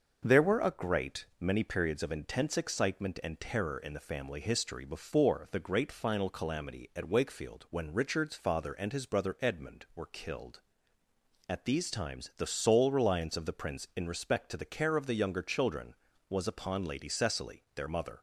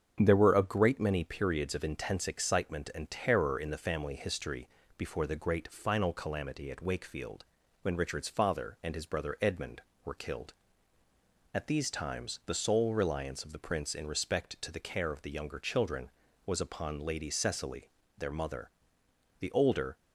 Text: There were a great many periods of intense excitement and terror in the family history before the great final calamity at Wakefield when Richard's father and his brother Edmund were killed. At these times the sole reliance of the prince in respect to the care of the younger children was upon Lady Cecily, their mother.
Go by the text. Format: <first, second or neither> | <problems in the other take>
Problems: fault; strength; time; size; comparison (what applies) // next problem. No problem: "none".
first | starts louder than the rest; strong; until 1.2 s; 7 dB; also in the first // pauses between "history" and "before"; slight; at 4.6 s; 0.30 s long // pauses between "Wakefield" and "when"; at 7.4 s; 0.38 s long // goes on to say "The older"; from 19.3 s on; 0.58 s long